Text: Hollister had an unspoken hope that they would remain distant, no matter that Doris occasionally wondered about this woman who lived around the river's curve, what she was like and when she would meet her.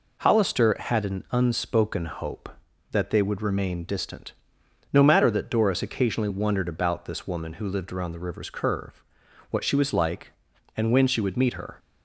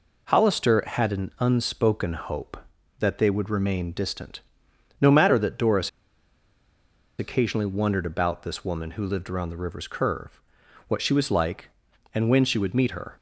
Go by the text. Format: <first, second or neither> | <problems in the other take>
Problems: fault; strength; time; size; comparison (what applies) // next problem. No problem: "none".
first | pauses between "Doris" and "occasionally"; strong; at 5.8 s; 1.3 s long